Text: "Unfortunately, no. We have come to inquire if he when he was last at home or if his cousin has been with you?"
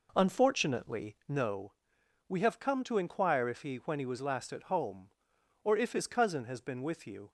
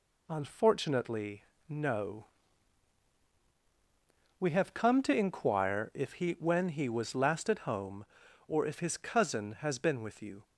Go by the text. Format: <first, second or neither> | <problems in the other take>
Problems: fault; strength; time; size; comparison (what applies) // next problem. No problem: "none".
second | starts louder than the rest; noticeable; until 1.5 s; 4.5 dB